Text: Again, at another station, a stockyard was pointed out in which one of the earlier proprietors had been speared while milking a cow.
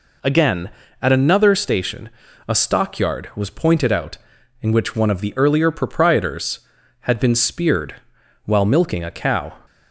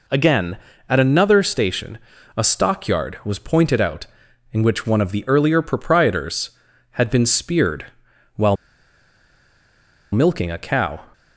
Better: first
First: pauses between "speared" and "while"; noticeable; at 7.9 s; 0.50 s long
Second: pauses between "speared" and "while"; noticeable; at 7.8 s; 0.50 s long // pauses between "while" and "milking"; strong; at 8.5 s; 1.5 s long

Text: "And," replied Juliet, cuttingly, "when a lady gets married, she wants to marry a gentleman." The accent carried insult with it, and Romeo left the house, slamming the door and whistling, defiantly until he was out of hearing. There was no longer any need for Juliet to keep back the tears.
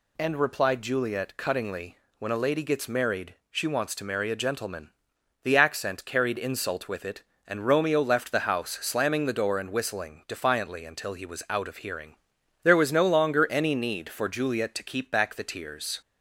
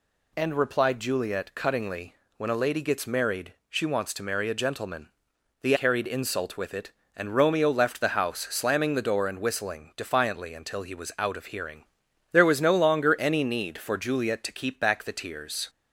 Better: first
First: none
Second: skips "accent"; at 5.7 s

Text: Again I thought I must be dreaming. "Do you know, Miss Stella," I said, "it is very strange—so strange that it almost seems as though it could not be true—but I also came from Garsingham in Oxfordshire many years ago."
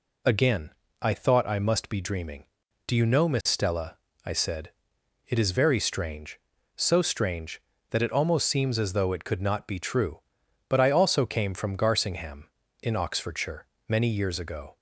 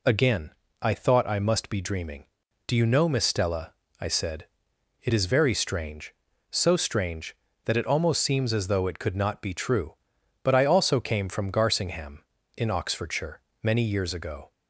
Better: neither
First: pauses between "Again" and "I"; slight; at 0.7 s; 0.30 s long // pauses between "Oxfordshire" and "many"; slight; at 13.6 s; 0.22 s long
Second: pauses between "Again" and "I"; slight; at 0.5 s; 0.30 s long // pauses between "Oxfordshire" and "many"; slight; at 13.4 s; 0.22 s long

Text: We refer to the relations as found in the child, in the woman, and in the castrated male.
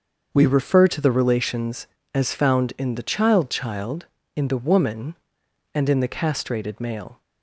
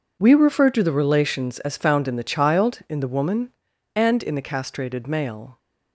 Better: second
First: starts louder than the rest; until 1.3 s; 6.5 dB // says "child" twice; at 3.4 s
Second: none

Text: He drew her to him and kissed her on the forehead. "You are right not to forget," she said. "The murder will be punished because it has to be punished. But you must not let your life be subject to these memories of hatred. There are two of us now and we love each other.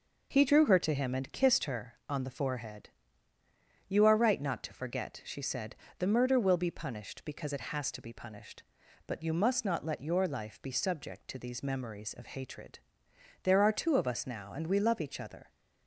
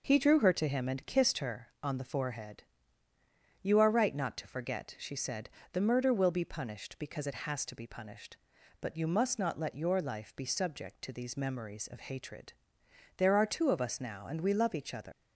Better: first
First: none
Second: leaves "other" unfinished; at 15.1 s; 110 ms

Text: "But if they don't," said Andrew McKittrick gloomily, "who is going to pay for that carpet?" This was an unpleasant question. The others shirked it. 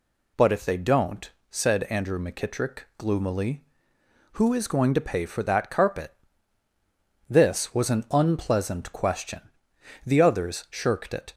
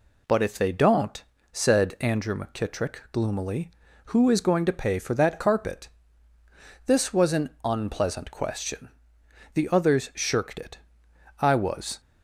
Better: first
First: none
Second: goes on to say "I was"; from 11.4 s on; 0.60 s long

